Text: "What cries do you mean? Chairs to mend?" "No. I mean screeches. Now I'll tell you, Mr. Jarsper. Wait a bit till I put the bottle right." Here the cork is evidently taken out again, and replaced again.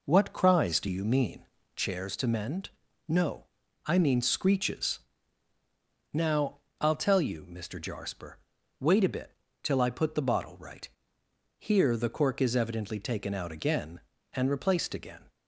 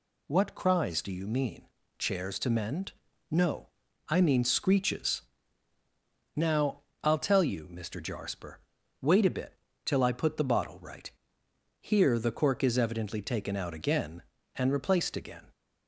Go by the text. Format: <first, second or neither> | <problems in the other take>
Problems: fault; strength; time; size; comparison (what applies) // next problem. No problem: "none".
second | starts louder than the rest; noticeable; until 1.8 s; 4 dB // pauses between "Now" and "I'll"; slight; at 6.5 s; 0.22 s long; slight in the second // pauses between "bit" and "till"; slight; at 9.3 s; 0.30 s long; slight in the second